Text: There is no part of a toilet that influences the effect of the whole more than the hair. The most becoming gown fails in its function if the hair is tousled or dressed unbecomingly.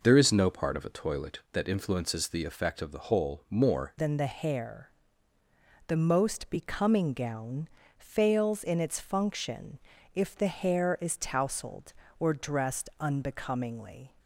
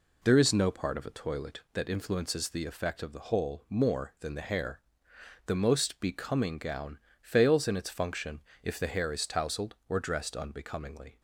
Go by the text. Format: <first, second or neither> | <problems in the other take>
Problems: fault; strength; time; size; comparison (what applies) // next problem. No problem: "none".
second | changes voice at "than"; from 3.9 s on; 10.2 s long // pauses between "gown" and "fails"; slight; at 7.6 s; 0.30 s long; slight in the second // pauses between "function" and "if"; at 9.7 s; 0.38 s long; slight in the second